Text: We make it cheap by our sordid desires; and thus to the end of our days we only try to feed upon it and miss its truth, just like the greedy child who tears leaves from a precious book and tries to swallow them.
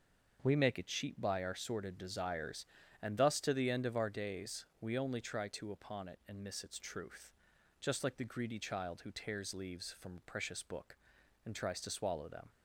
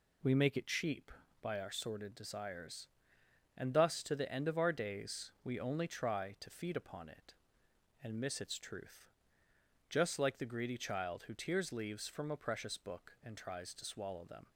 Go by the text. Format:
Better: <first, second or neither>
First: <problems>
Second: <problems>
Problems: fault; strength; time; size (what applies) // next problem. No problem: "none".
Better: second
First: starts louder than the rest; noticeable; until 1.4 s; 6 dB // pauses between "days" and "we"; slight; at 4.6 s; 0.16 s long // skips "feed"; at 5.7 s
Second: none